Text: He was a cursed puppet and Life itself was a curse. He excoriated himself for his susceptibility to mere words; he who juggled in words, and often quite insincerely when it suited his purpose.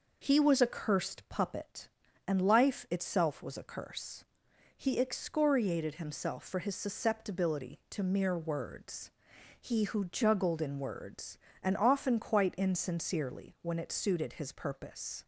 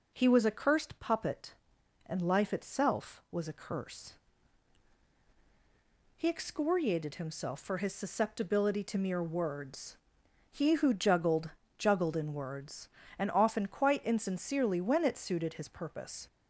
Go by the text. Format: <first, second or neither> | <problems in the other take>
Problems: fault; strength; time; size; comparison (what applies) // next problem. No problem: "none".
first | says "juggled" twice; at 11.7 s